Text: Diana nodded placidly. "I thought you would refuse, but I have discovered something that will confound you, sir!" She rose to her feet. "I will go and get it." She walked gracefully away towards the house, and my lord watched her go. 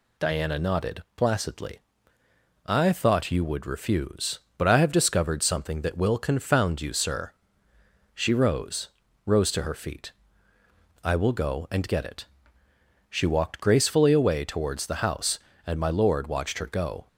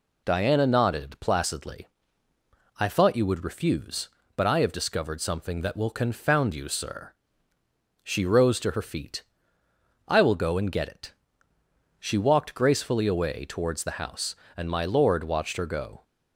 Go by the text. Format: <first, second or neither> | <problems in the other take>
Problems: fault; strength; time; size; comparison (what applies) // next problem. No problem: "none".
second | says "rose" twice; at 9.2 s